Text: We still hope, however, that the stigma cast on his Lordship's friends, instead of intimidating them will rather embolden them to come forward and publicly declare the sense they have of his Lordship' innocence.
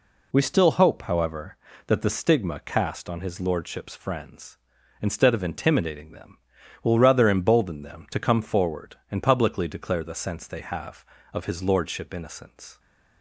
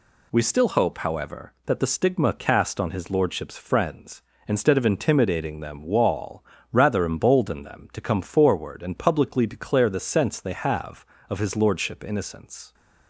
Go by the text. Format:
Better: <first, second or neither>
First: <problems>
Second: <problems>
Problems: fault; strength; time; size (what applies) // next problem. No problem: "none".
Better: first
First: none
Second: says "wall" for "will"; at 5.8 s